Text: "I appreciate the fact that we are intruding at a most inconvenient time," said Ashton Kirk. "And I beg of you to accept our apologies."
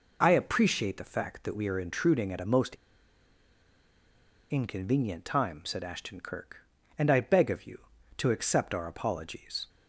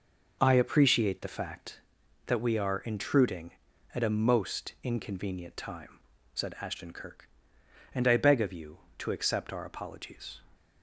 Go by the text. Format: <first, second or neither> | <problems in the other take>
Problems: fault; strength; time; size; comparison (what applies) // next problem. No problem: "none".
second | pauses between "most" and "inconvenient"; strong; at 2.7 s; 1.7 s long